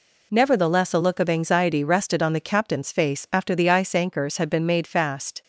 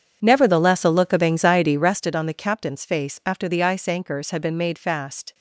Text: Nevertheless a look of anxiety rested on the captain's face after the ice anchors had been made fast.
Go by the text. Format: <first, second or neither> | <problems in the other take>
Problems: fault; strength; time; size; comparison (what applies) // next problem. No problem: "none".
first | starts louder than the rest; strong; until 2.1 s; 7.5 dB